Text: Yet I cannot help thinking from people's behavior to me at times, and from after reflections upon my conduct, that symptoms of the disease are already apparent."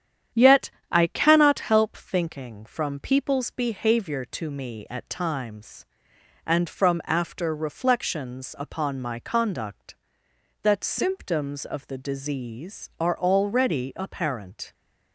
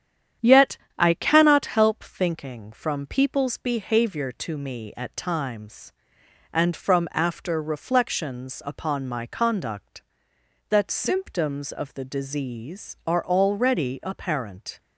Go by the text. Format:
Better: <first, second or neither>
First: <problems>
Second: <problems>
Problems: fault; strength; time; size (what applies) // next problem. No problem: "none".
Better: neither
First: starts louder than the rest; strong; until 1.5 s; 9.5 dB // pauses between "Yet" and "I"; slight; at 0.6 s; 0.20 s long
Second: starts louder than the rest; strong; until 1.6 s; 9.5 dB // pauses between "Yet" and "I"; slight; at 0.7 s; 0.20 s long